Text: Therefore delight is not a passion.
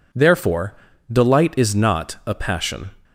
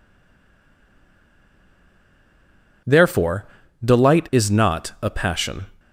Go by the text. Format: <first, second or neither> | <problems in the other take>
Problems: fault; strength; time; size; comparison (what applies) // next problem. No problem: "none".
first | stays silent before the first word; strong; until 2.8 s; 2.8 s long // pauses between "Therefore" and "delight"; at 3.4 s; 0.38 s long; also in the first